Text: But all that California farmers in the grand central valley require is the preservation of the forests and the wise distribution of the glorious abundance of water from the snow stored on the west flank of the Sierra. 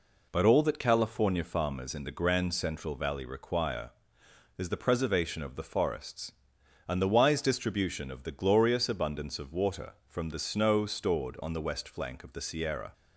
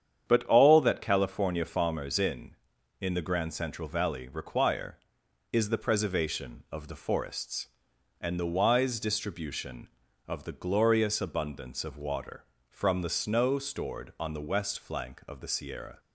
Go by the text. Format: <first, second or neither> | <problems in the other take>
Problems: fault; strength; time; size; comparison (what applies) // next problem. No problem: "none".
first | starts louder than the rest; strong; until 1.2 s; 8.5 dB // says "in" twice; at 2.9 s